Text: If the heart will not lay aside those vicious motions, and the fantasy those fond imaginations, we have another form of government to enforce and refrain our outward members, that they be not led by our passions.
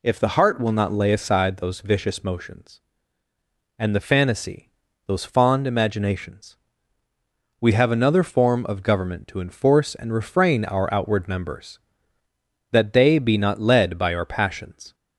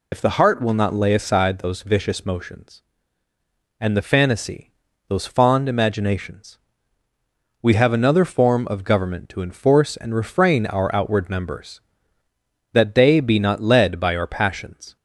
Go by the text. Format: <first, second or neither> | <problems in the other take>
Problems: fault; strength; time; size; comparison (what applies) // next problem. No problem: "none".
first | loses the start of "If"; at 0.1 s; 85 ms // pauses between "fantasy" and "those"; slight; at 4.7 s; 0.36 s long; slight in the first